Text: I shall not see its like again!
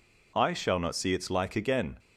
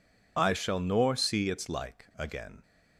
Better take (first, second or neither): first